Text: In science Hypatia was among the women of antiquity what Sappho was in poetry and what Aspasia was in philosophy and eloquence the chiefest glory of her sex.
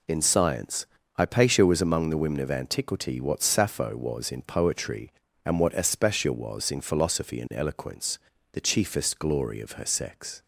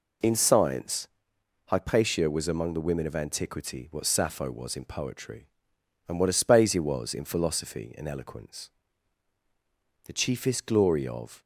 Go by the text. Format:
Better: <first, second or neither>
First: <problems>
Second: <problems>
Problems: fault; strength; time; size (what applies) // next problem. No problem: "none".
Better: first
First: pauses between "science" and "Hypatia"; slight; at 0.8 s; 0.28 s long // pauses between "eloquence" and "the"; slight; at 8.2 s; 0.32 s long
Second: pauses between "science" and "Hypatia"; noticeable; at 1.0 s; 0.60 s long // pauses between "eloquence" and "the"; strong; at 8.6 s; 1.3 s long // stops before "her sex"; at 11.4 s